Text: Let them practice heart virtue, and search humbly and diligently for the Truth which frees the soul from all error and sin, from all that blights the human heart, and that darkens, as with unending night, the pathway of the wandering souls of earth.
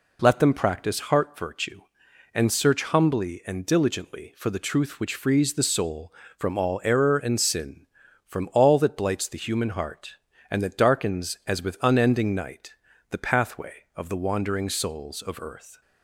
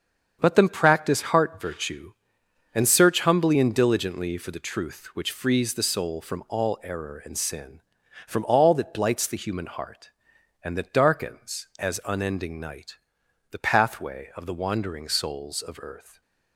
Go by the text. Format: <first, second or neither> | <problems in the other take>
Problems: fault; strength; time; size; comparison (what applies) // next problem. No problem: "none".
first | starts louder than the rest; strong; until 1.4 s; 7.5 dB // skips "with"; at 12.0 s